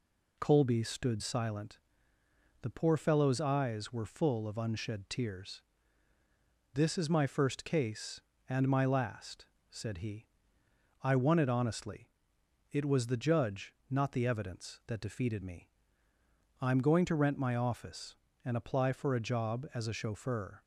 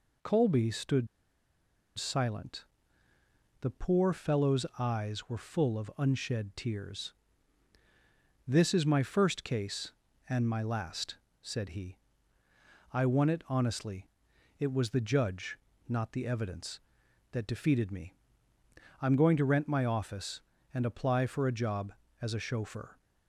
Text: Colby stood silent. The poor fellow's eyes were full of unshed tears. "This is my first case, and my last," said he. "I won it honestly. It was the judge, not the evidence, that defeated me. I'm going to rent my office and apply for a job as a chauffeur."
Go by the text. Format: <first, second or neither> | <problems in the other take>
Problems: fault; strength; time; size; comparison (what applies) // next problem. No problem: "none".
first | pauses between "stood" and "silent"; noticeable; at 1.0 s; 0.91 s long